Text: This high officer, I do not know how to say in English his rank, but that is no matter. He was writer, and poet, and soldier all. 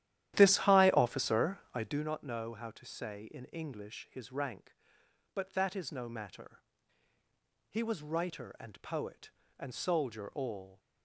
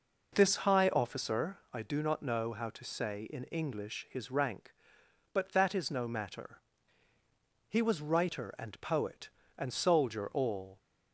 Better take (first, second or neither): second